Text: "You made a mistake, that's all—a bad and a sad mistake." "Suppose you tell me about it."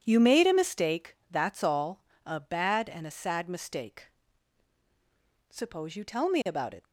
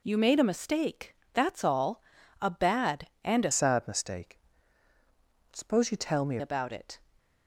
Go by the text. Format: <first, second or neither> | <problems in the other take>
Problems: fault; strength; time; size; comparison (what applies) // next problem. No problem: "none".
first | changes voice from "sad" to "me"; from 3.5 to 6.3 s; 2.8 s long